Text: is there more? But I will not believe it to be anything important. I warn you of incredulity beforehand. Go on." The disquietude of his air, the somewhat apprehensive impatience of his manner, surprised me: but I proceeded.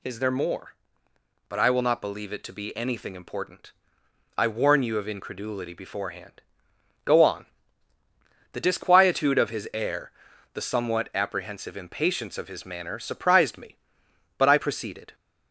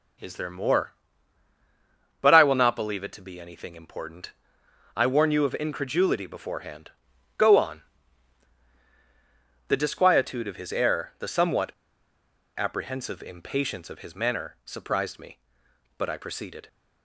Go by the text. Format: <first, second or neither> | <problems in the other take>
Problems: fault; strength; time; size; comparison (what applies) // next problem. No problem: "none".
first | pauses between "somewhat" and "apprehensive"; noticeable; at 11.7 s; 0.85 s long